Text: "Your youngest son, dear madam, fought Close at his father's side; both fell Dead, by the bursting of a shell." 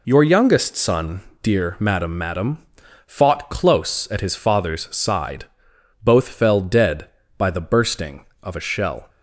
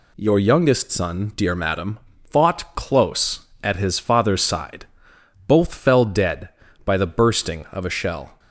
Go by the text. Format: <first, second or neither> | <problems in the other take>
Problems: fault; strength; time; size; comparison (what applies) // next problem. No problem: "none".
second | says "madam" twice; at 2.1 s